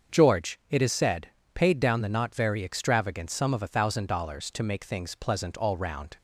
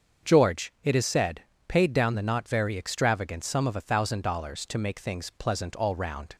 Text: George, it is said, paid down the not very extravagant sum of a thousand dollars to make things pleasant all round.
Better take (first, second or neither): neither